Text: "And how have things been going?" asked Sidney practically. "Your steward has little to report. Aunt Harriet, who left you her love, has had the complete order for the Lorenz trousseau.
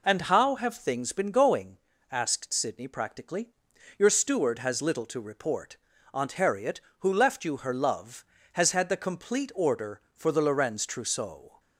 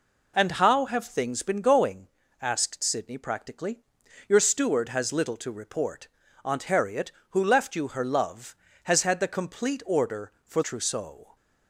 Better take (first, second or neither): first